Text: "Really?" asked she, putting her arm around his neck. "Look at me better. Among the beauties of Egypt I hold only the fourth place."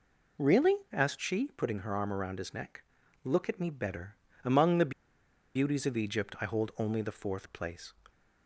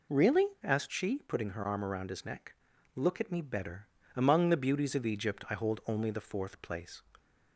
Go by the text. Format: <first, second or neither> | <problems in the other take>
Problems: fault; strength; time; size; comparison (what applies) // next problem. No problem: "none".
second | pauses between "the" and "beauties"; noticeable; at 4.9 s; 0.64 s long